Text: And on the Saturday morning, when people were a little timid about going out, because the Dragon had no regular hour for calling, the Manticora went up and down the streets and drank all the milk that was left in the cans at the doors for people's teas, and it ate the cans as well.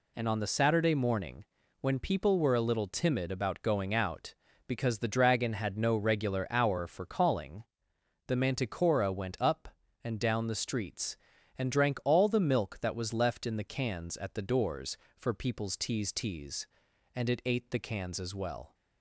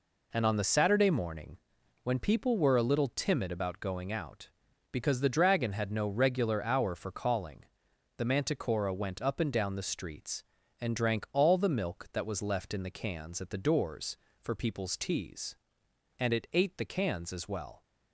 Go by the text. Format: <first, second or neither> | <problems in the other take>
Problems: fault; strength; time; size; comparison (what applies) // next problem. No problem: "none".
second | says "teas" twice; at 16.1 s